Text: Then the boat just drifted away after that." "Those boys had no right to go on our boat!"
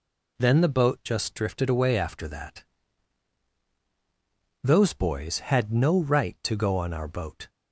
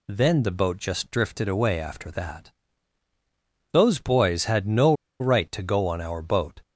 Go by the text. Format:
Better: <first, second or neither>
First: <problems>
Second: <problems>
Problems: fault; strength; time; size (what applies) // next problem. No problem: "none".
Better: first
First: none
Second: pauses between "no" and "right"; slight; at 4.9 s; 0.26 s long